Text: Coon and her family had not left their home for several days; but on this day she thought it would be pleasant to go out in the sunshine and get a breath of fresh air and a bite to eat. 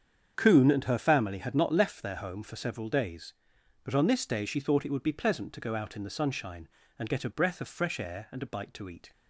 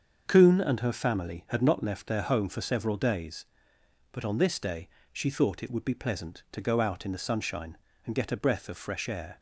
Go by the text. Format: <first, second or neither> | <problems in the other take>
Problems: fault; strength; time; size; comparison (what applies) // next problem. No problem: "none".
first | starts louder than the rest; until 1.2 s; 7 dB; strong in the first // pauses between "day" and "she"; slight; at 4.8 s; 0.24 s long // stops before "and a bite to eat"; at 9.3 s